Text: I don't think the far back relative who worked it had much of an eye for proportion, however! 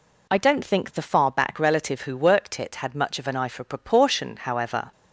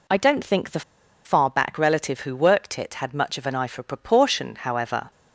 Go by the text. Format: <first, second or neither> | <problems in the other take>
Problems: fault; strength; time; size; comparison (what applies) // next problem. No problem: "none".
first | pauses between "the" and "far"; at 0.8 s; 0.44 s long